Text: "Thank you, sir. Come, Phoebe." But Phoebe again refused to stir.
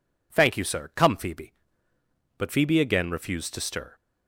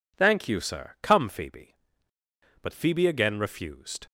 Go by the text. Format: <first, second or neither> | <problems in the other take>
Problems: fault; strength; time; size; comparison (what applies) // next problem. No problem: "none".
first | stops before "to stir"; at 4.0 s